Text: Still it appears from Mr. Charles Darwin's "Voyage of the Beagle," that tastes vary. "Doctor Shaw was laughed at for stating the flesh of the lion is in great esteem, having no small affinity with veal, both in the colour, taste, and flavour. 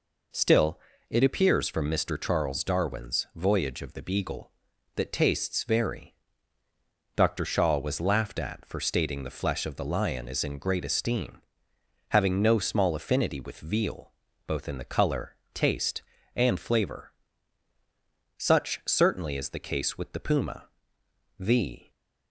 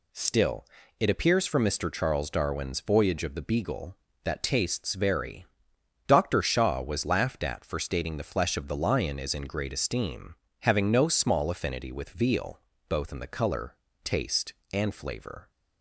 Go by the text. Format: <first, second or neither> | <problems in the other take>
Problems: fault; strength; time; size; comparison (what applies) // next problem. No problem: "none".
second | pauses between "Still" and "it"; slight; at 0.8 s; 0.30 s long; slight in the second // goes on to say "Such certainly is the case with the puma The"; strong; from 18.3 s on; 3.5 s long